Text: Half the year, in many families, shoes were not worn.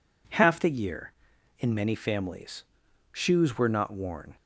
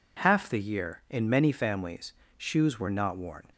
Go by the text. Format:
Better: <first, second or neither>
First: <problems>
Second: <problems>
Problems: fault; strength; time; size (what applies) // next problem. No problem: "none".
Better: neither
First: none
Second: none